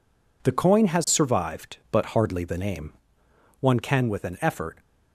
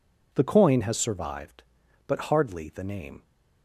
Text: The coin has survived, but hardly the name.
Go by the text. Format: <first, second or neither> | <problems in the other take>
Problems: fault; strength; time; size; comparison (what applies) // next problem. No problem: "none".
second | goes on to say "One can with an effort"; noticeable; from 3.6 s on; 1.1 s long